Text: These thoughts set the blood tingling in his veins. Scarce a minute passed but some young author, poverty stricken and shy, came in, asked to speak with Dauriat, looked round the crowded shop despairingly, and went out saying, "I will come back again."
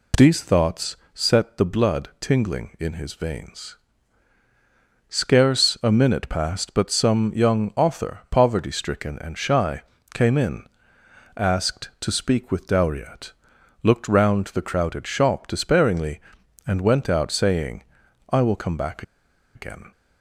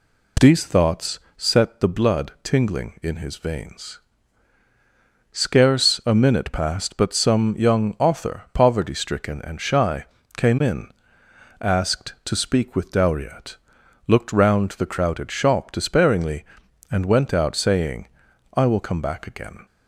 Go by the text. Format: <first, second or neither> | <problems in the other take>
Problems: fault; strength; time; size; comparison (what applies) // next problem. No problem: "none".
second | pauses between "thoughts" and "set"; slight; at 0.9 s; 0.18 s long; slight in the second // pauses between "back" and "again"; noticeable; at 19.0 s; 0.52 s long